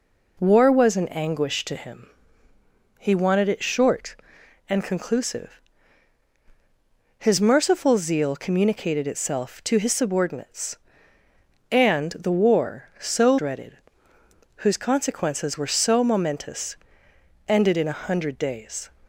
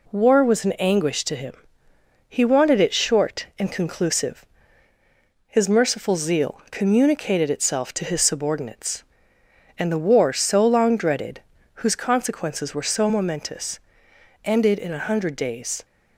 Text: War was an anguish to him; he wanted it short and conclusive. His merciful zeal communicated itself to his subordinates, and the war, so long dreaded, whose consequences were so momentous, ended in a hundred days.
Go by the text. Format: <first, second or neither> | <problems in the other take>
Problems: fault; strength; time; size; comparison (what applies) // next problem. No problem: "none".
second | skips "long"; at 13.3 s